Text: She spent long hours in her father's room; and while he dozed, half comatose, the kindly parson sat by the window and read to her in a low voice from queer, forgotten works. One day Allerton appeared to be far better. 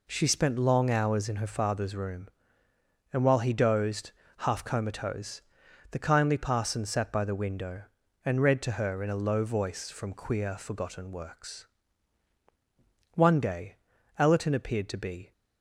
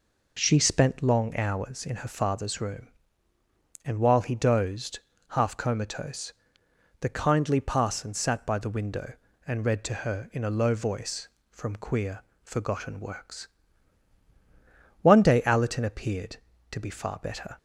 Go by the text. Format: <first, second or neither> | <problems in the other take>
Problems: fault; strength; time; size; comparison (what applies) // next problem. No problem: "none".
second | pauses between "day" and "Allerton"; at 13.7 s; 0.42 s long // stops before "far better"; at 15.3 s